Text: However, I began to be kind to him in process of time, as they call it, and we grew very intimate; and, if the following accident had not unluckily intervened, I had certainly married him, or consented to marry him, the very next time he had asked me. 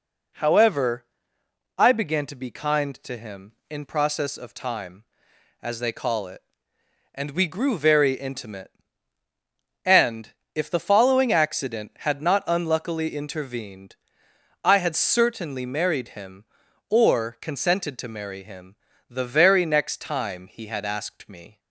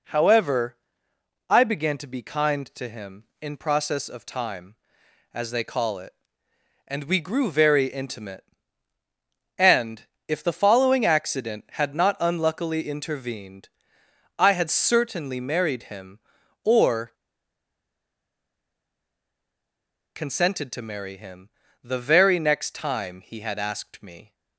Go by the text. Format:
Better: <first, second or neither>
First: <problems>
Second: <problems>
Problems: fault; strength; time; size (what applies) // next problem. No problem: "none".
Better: first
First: none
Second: pauses between "or" and "consented"; strong; at 17.0 s; 3.0 s long